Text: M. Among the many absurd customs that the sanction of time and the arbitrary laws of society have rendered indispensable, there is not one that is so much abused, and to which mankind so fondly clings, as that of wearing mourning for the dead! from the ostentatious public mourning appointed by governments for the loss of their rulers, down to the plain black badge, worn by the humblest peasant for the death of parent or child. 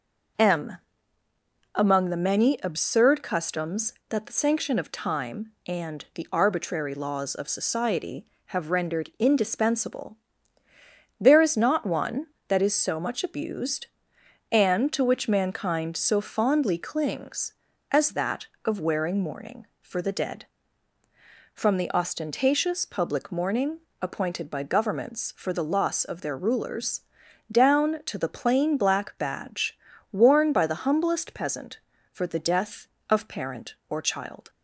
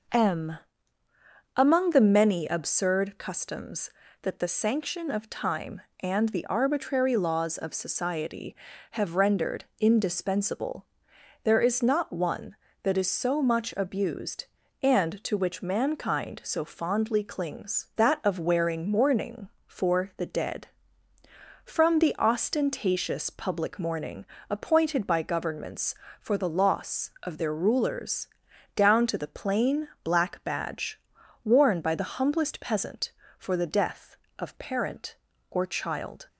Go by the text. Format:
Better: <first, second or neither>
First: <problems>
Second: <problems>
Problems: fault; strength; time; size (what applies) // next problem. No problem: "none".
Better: first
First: pauses between "mourning" and "appointed"; slight; at 23.7 s; 0.22 s long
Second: skips "as"; at 17.9 s // pauses between "mourning" and "appointed"; slight; at 24.2 s; 0.26 s long